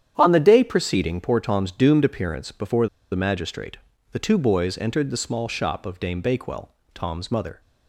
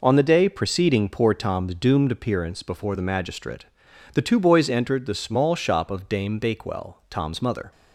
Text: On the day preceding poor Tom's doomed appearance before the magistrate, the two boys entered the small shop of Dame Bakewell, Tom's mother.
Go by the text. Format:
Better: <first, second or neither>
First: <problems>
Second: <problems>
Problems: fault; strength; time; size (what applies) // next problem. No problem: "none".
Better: second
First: starts louder than the rest; strong; until 1.1 s; 9.5 dB // pauses between "before" and "the"; slight; at 2.8 s; 0.24 s long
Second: none